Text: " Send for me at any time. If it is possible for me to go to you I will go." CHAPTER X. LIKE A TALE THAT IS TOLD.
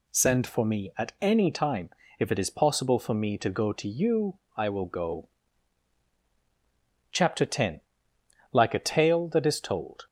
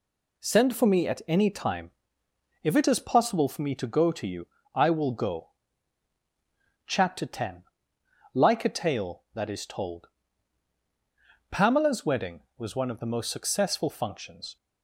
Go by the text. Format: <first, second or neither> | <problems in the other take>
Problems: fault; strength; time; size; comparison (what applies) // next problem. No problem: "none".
first | pauses between "you" and "I"; slight; at 4.4 s; 0.26 s long; slight in the first // goes on to say "PAMELA'S wedding was one of the most successful functions"; strong; from 11.5 s on; 3.0 s long